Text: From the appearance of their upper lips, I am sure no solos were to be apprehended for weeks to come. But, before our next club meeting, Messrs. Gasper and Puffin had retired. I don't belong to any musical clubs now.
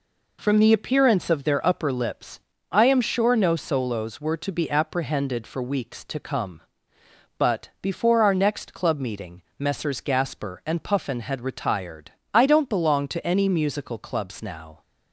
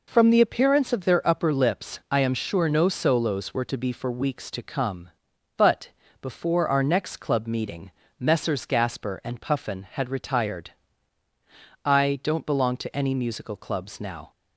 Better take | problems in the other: first | skips "apprehended"; at 3.9 s

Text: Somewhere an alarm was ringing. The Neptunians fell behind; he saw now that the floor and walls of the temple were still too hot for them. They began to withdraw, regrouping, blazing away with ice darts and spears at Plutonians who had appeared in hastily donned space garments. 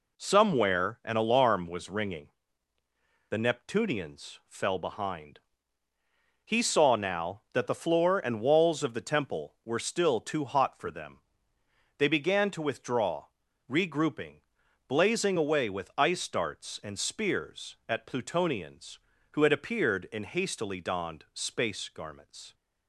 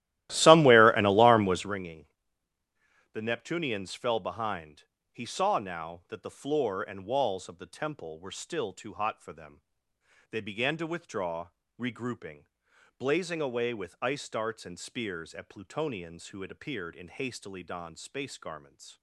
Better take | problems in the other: first | starts louder than the rest; strong; until 1.8 s; 15 dB

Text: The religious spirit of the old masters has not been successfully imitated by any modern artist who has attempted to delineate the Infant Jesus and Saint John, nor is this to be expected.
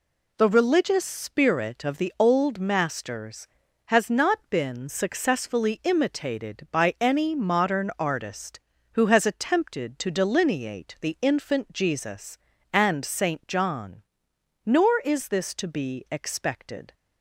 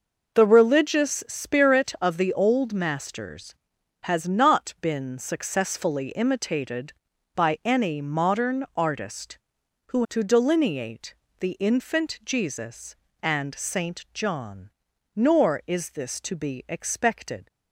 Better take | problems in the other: first | skips "has attempted"; at 10.0 s // pauses between "delineate" and "the"; slight; at 11.1 s; 0.26 s long

